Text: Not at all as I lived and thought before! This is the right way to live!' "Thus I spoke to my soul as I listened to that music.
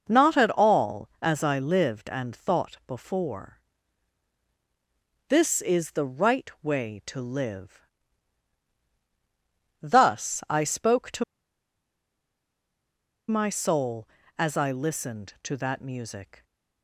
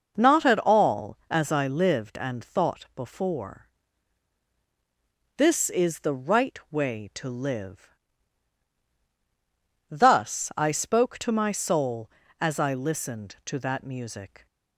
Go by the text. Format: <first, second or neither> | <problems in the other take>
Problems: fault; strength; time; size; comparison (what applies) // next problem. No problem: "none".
second | pauses between "to" and "my"; strong; at 11.2 s; 2.0 s long